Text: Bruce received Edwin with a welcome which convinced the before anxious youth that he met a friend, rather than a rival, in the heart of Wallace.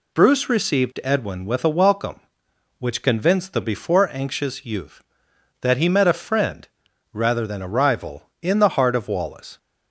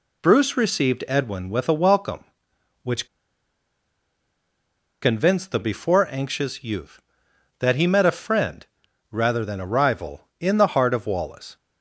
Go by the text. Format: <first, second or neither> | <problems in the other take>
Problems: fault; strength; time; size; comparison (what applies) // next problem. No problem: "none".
first | pauses between "which" and "convinced"; strong; at 3.0 s; 1.9 s long